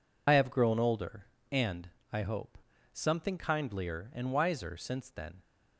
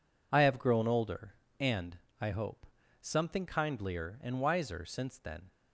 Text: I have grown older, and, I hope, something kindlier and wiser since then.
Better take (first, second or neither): second